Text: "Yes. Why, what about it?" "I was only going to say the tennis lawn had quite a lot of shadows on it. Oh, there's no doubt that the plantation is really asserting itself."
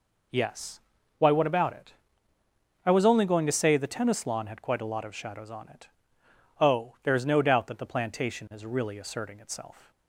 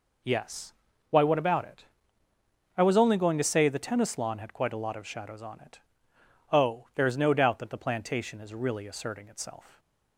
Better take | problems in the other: neither | none

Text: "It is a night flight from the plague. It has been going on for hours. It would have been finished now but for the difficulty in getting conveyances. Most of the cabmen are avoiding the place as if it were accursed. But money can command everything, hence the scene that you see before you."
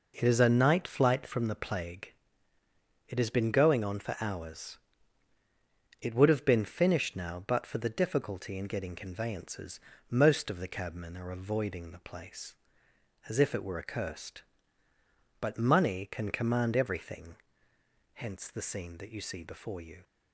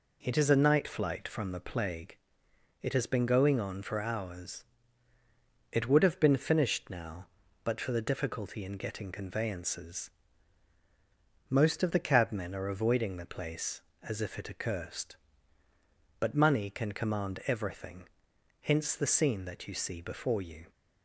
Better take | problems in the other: first | skips "were"; at 14.4 s

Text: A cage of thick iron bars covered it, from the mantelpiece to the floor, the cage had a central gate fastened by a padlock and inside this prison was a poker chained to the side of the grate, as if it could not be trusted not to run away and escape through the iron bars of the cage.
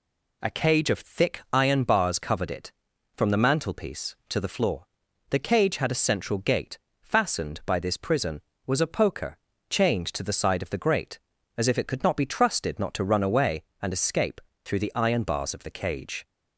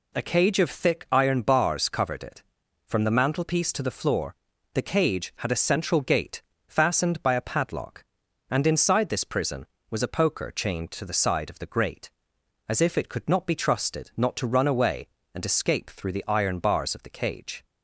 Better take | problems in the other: second | pauses between "gate" and "fastened"; slight; at 6.7 s; 0.24 s long; slight in the second // skips "a padlock and inside"; at 7.7 s // pauses between "poker" and "chained"; slight; at 9.3 s; 0.32 s long // pauses between "escape" and "through"; slight; at 14.3 s; 0.24 s long

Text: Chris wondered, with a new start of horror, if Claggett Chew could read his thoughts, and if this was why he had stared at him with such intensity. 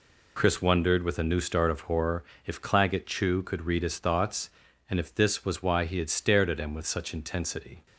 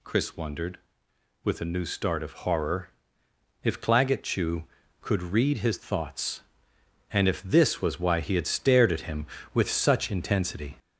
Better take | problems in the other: first | gets louder; throughout; 3.5 dB

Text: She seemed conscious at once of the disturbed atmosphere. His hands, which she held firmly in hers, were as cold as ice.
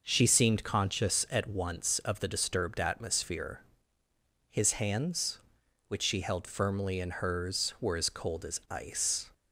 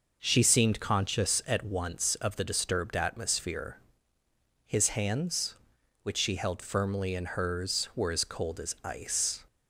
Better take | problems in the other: neither | none

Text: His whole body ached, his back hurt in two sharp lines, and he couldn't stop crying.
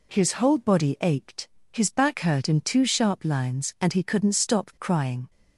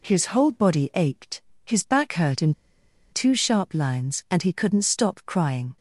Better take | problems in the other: first | pauses between "in" and "two"; noticeable; at 2.5 s; 0.57 s long

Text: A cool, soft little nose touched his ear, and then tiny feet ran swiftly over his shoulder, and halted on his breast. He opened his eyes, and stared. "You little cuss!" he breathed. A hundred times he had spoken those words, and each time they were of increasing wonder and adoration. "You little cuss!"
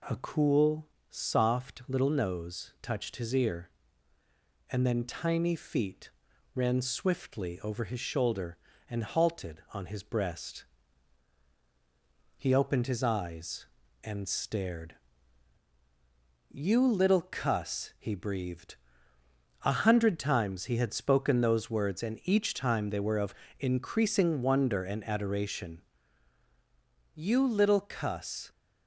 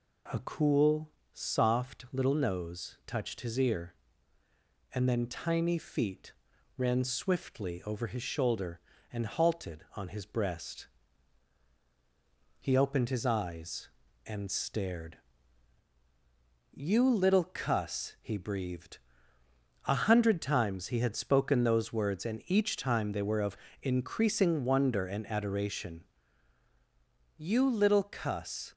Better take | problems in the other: neither | pauses between "feet" and "ran"; noticeable; the same in both // pauses between "of" and "increasing"; slight; the same in both

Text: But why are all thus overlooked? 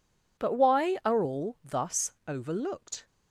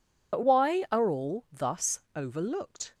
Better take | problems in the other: first | loses the start of "But"; at 0.3 s; 65 ms // pauses between "thus" and "overlooked"; slight; at 1.9 s; 0.16 s long; slight in the first

